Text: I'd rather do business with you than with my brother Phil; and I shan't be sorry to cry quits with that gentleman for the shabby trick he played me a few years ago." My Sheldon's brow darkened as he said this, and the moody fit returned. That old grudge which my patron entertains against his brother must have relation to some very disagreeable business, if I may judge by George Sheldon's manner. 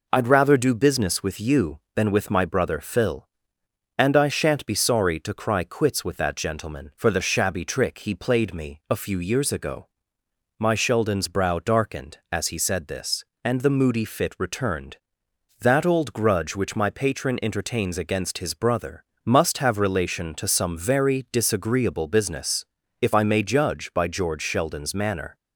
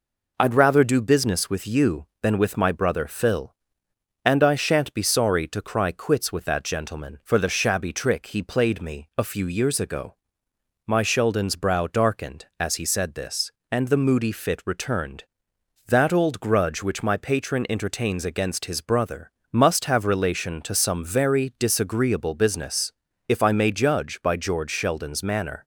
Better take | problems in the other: neither | pauses between "brother" and "must"; slight; the same in both

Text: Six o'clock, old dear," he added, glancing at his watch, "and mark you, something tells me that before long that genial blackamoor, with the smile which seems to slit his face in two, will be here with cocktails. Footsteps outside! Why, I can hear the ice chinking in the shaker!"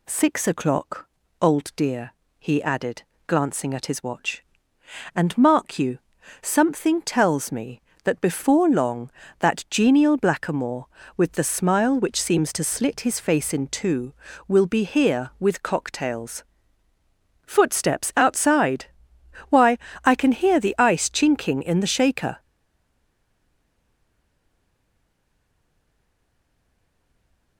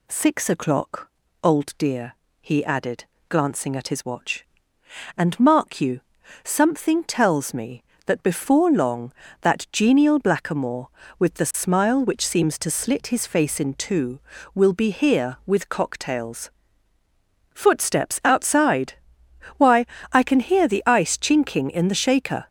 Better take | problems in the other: second | stays silent after the last word; strong; from 22.3 s on; 5.2 s long

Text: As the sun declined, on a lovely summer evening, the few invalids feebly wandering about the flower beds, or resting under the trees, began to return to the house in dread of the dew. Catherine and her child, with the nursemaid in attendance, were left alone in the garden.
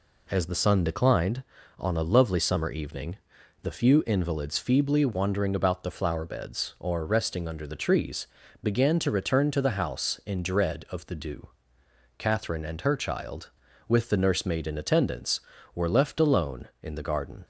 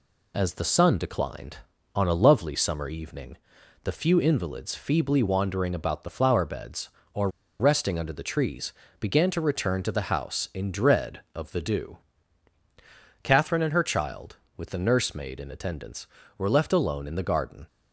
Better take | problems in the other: first | pauses between "or" and "resting"; slight; at 7.2 s; 0.30 s long

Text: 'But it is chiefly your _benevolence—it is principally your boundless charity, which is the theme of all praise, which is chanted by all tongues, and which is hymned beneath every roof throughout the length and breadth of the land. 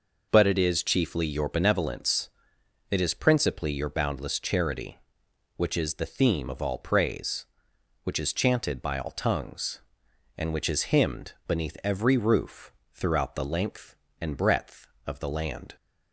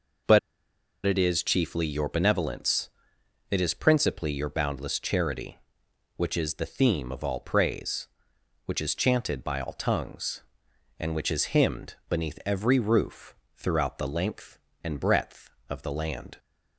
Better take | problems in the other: first | pauses between "But" and "it"; noticeable; at 0.3 s; 0.67 s long // pauses between "roof" and "throughout"; slight; at 13.3 s; 0.20 s long; slight in the first

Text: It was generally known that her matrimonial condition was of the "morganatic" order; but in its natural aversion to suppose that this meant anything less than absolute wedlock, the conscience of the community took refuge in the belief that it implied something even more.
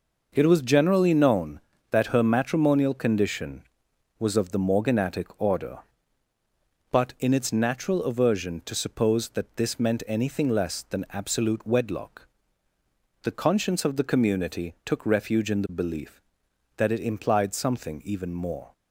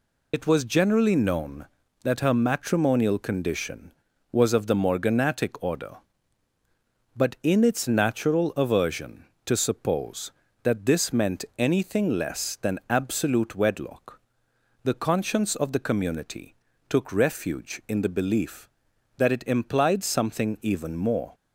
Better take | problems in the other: first | loses the start of "It"; at 0.3 s; 65 ms // pauses between "community" and "took"; slight; at 16.5 s; 0.32 s long

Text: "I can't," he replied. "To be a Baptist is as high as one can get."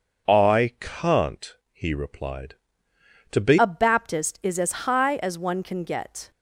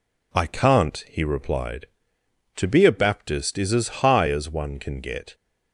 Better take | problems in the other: second | changes voice at "a"; from 3.5 s on; 2.8 s long

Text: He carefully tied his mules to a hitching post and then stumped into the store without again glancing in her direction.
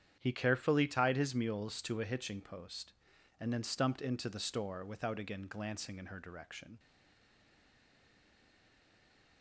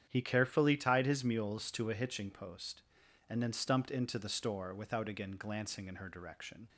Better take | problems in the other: second | starts louder than the rest; strong; until 1.2 s; 9 dB; strong in the second // stays silent after the last word; strong; from 6.7 s on; 2.7 s long

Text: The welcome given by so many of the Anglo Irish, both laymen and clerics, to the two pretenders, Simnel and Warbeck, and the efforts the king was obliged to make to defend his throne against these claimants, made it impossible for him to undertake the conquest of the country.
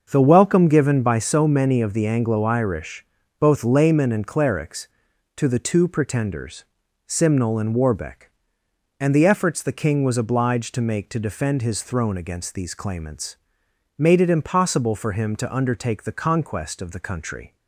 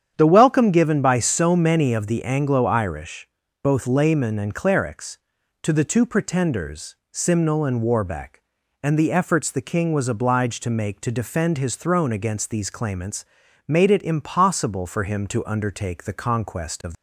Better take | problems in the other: first | starts louder than the rest; strong; until 1.1 s; 8.5 dB; also in the first // stops before "the country"; at 16.9 s

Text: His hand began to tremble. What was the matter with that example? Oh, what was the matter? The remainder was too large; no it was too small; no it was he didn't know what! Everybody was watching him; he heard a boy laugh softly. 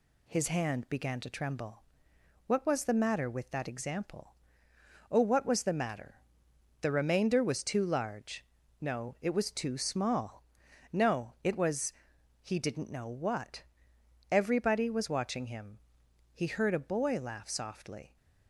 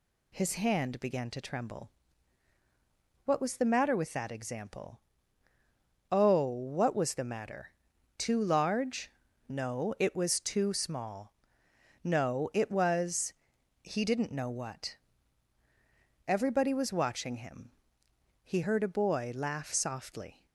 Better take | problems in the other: first | skips "The remainder was"; at 7.9 s // pauses between "was" and "he"; noticeable; at 13.3 s; 0.50 s long; noticeable in the first

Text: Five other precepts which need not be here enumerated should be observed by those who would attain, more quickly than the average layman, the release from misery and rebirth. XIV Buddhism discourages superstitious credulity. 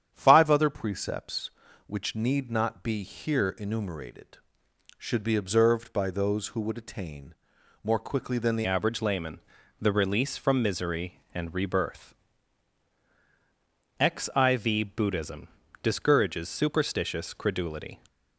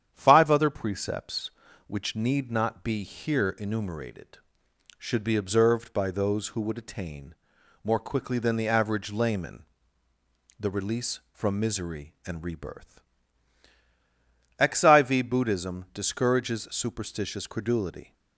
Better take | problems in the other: second | starts louder than the rest; strong; until 1.1 s; 9 dB; strong in the second // changes voice at "average"; from 8.6 s on; 9.3 s long // pauses between "Buddhism" and "discourages"; slight; at 15.4 s; 0.36 s long

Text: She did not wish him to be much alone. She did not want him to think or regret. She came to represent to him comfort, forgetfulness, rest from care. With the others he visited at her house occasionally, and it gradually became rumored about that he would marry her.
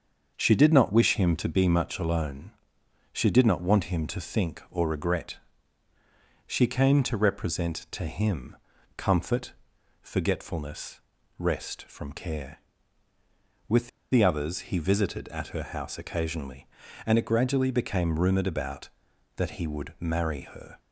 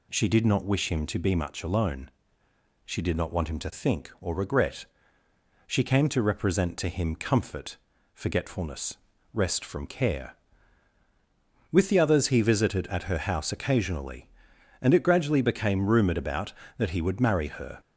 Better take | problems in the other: second | starts louder than the rest; until 1.3 s; 6.5 dB // pauses between "him" and "comfort"; at 8.5 s; 0.40 s long // pauses between "With" and "the"; slight; at 13.8 s; 0.23 s long

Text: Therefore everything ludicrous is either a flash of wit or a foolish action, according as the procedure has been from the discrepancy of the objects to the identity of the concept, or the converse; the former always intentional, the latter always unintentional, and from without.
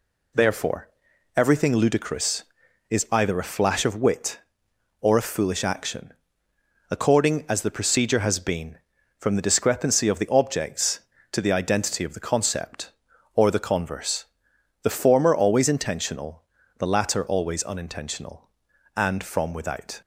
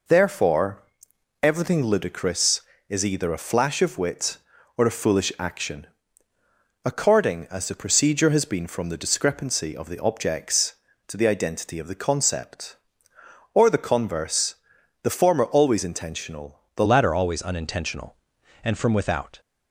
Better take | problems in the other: first | pauses between "Therefore" and "everything"; noticeable; at 0.8 s; 0.60 s long; noticeable in the first // changes voice at "latter"; from 16.8 s on; 2.6 s long

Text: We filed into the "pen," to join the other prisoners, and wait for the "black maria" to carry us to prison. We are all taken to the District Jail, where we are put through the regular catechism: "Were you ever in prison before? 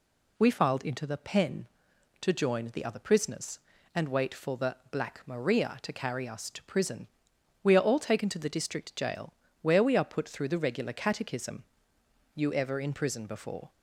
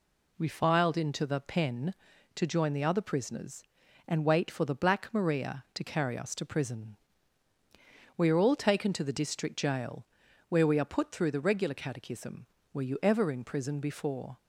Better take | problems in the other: second | pauses between "the" and "black"; slight; at 4.7 s; 0.16 s long // skips "Were"; at 11.9 s

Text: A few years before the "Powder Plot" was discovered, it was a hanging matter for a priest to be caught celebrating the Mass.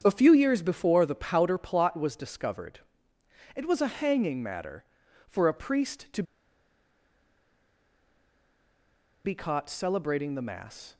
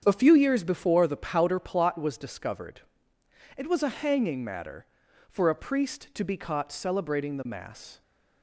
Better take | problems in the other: second | starts louder than the rest; strong; until 1.0 s; 8 dB; strong in the second // pauses between "to" and "be"; strong; at 6.2 s; 3.0 s long

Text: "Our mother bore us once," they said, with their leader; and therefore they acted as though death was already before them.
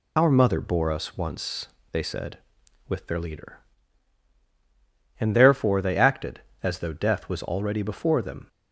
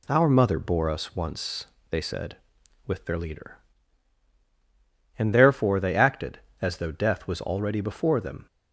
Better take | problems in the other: second | loses the start of "Our"; at 0.1 s; 115 ms

